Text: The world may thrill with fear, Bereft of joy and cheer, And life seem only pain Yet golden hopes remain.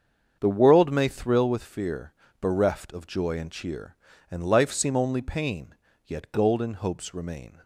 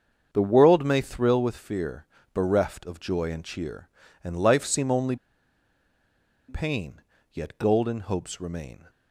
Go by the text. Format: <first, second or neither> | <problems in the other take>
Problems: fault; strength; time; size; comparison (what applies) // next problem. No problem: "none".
first | starts louder than the rest; strong; until 1.3 s; 7 dB; strong in the first // pauses between "only" and "pain"; strong; at 5.1 s; 1.3 s long // pauses between "pain" and "Yet"; slight; at 7.0 s; 0.32 s long; slight in the first